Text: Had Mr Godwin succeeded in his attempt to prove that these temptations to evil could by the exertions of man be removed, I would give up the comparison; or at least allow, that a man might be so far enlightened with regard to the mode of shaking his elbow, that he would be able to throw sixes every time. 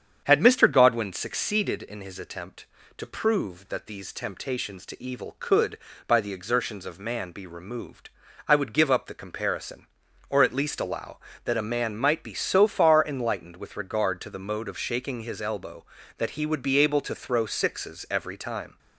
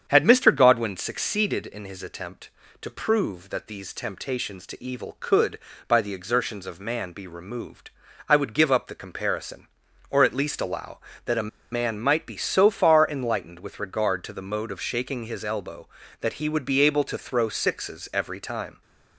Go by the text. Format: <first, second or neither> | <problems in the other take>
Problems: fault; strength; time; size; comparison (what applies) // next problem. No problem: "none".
first | starts louder than the rest; strong; until 1.0 s; 8 dB; strong in the first // pauses between "a" and "man"; slight; at 11.4 s; 0.23 s long